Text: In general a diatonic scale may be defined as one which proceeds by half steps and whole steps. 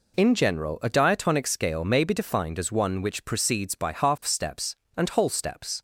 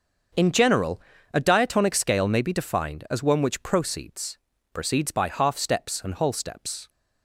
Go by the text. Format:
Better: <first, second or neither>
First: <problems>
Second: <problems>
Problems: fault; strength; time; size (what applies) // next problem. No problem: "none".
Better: first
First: none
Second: starts louder than the rest; until 1.7 s; 6.5 dB // pauses between "general" and "a"; slight; at 1.0 s; 0.34 s long // says "proceeds" twice; at 4.7 s